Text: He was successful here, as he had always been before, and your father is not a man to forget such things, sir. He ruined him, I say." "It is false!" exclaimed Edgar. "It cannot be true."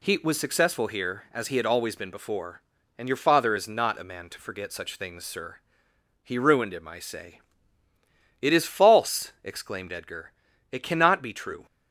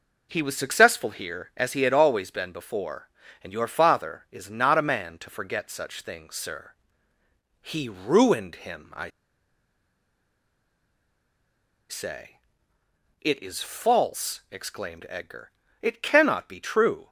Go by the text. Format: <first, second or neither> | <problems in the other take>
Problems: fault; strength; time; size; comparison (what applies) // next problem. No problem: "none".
first | pauses between "I" and "say"; strong; at 9.0 s; 2.7 s long